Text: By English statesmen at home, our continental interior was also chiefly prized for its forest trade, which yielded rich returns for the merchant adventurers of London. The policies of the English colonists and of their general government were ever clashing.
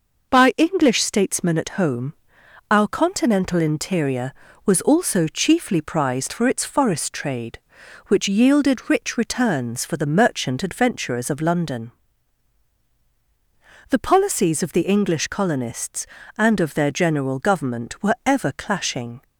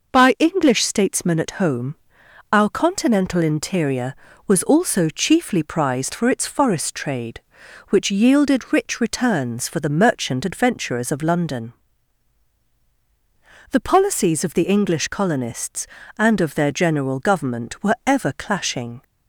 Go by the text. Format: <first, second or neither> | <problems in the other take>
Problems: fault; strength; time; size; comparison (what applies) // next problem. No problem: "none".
neither | none